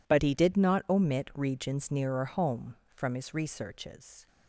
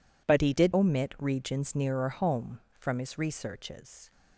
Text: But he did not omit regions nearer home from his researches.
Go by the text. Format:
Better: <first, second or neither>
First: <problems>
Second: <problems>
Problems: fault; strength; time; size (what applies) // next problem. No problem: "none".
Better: first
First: none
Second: skips "not"; at 0.7 s